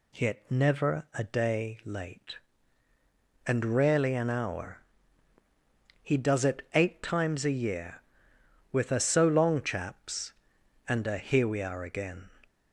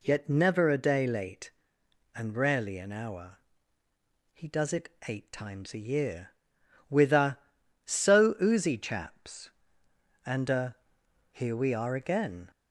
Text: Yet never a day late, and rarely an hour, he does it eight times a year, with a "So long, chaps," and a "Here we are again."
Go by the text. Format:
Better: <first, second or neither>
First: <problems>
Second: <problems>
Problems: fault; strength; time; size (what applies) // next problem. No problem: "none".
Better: first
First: none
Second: pauses between "it" and "eight"; slight; at 4.8 s; 0.18 s long // says "oozy" for "long"; at 8.4 s // pauses between "a" and "Here"; noticeable; at 10.7 s; 0.56 s long